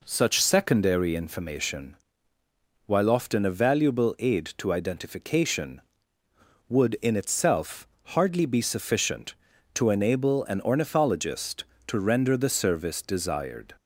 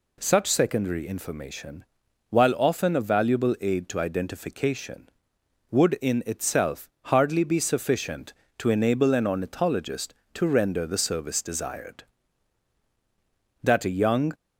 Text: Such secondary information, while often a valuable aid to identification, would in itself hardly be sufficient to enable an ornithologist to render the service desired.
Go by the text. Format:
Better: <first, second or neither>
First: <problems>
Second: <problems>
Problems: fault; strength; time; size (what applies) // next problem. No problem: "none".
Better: first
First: pauses between "itself" and "hardly"; slight; at 7.8 s; 0.20 s long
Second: pauses between "itself" and "hardly"; slight; at 6.8 s; 0.16 s long // goes on to say "That a young"; noticeable; from 13.6 s on; 0.70 s long